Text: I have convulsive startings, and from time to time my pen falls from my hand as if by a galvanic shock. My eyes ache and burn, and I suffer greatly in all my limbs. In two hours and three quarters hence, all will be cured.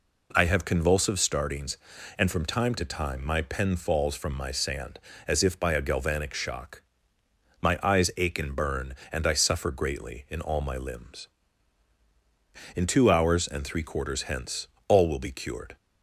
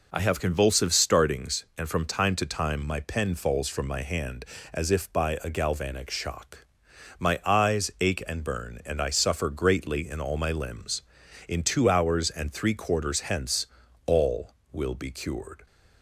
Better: second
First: says "sand" for "hand"; at 4.5 s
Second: none

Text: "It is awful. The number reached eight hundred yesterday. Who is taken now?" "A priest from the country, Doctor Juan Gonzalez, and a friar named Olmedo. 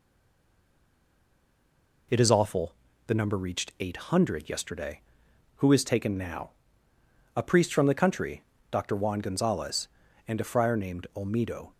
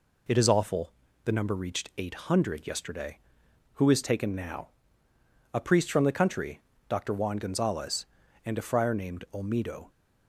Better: second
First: stays silent before the first word; noticeable; until 2.0 s; 2.0 s long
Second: none

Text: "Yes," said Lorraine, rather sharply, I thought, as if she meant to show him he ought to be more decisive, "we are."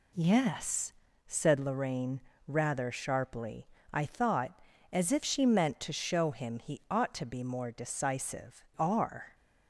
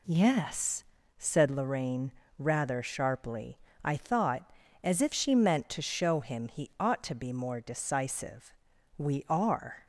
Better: second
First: skips "we"; at 8.7 s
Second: none

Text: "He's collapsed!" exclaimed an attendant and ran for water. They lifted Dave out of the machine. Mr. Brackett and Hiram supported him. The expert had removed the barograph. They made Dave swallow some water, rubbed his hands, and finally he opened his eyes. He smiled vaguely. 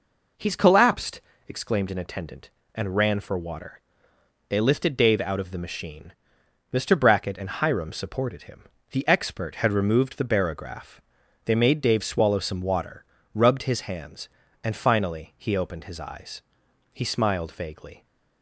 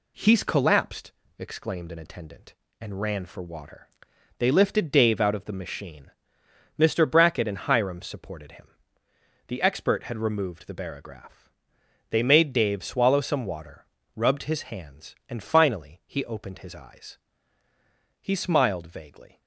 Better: neither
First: none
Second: none

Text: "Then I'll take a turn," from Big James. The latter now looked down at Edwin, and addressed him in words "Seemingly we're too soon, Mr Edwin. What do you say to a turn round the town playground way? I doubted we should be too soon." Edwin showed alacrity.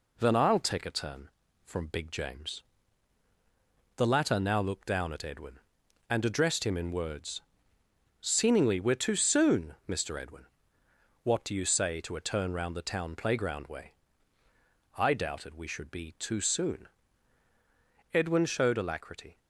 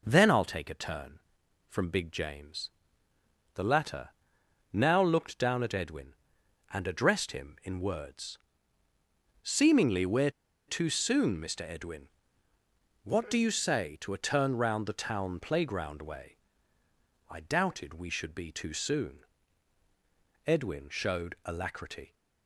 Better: first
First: pauses between "words" and "Seemingly"; noticeable; at 7.4 s; 0.78 s long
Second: pauses between "latter" and "now"; noticeable; at 4.1 s; 0.62 s long // pauses between "words" and "Seemingly"; at 8.3 s; 1.0 s long // pauses between "we're" and "too"; at 10.3 s; 0.37 s long

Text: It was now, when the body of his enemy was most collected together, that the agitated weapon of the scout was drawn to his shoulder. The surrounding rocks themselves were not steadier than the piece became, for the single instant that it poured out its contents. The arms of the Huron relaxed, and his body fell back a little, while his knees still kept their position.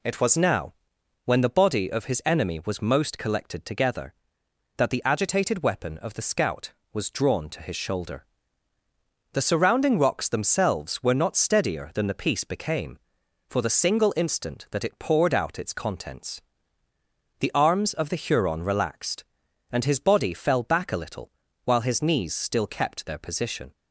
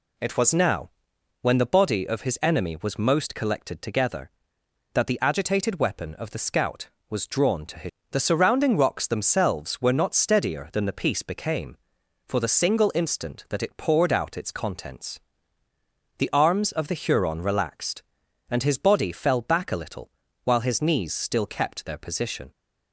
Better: first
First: none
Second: skips "shoulder"; at 8.0 s

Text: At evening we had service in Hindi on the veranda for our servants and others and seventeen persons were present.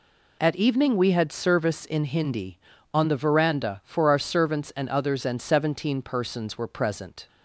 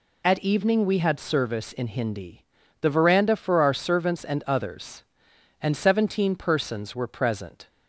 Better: first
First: none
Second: skips "on"; at 2.6 s

